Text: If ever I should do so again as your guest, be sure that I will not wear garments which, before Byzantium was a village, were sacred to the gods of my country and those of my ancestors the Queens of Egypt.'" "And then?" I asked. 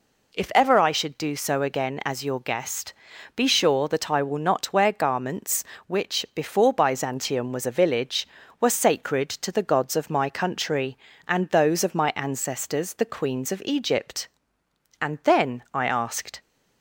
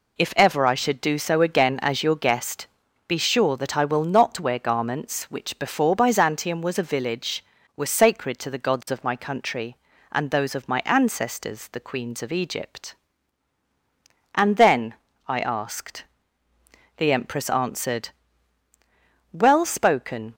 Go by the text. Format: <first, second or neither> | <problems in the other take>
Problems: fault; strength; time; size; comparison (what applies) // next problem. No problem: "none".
first | goes on to say "The Empress answered Well spoken"; strong; from 16.9 s on; 3.3 s long